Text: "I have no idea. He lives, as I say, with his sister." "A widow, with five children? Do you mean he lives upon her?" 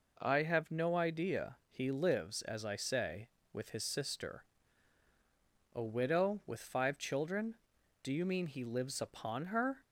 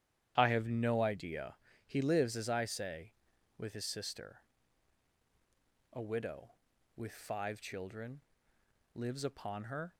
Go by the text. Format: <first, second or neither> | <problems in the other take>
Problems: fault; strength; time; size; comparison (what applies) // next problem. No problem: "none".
first | starts louder than the rest; strong; until 1.3 s; 10 dB // skips "Do you mean he"; at 8.5 s